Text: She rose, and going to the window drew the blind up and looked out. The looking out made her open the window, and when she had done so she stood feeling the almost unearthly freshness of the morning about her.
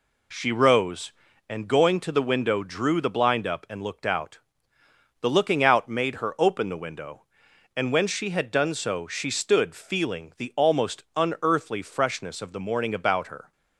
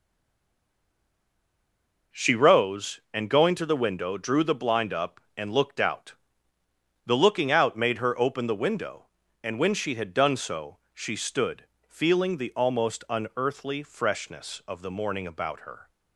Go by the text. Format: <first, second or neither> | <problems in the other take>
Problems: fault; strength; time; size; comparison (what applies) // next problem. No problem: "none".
first | stays silent before the first word; until 2.1 s; 2.1 s long // pauses between "stood" and "feeling"; slight; at 11.6 s; 0.20 s long